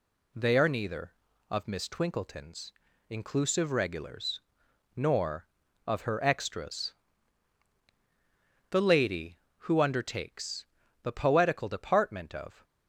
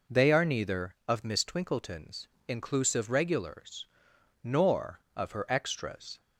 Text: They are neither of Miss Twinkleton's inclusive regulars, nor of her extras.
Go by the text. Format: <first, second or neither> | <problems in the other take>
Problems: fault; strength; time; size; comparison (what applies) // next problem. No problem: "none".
second | pauses between "Twinkleton's" and "inclusive"; at 2.7 s; 0.38 s long; slight in the second // goes on to say "The lady who undertakes the poetical department of"; strong; from 8.6 s on; 3.9 s long